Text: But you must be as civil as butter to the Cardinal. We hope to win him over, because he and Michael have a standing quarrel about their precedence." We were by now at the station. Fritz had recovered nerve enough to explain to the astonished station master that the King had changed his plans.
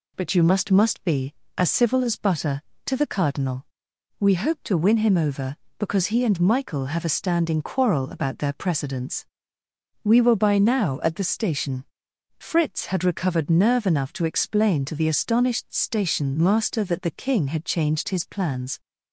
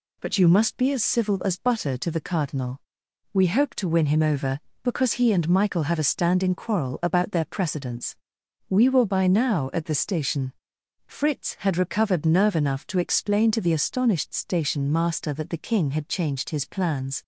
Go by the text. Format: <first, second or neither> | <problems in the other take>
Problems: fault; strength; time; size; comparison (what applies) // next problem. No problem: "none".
second | says "must" twice; at 0.6 s